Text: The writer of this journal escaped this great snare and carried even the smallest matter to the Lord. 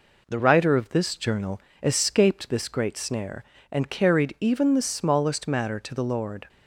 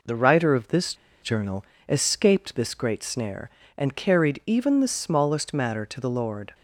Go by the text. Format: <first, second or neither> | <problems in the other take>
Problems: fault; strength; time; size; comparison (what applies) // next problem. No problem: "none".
first | pauses between "this" and "journal"; slight; at 0.9 s; 0.27 s long // pauses between "journal" and "escaped"; slight; at 1.6 s; 0.24 s long; slight in the first